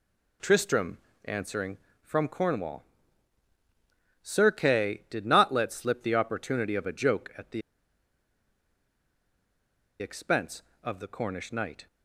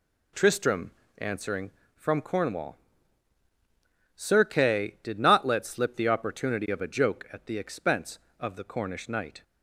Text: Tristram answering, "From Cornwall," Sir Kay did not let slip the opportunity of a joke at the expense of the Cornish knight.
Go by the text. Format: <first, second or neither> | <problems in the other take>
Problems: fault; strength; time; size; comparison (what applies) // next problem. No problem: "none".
second | pauses between "Tristram" and "answering"; slight; at 0.9 s; 0.28 s long; slight in the second // pauses between "the" and "expense"; strong; at 7.6 s; 2.3 s long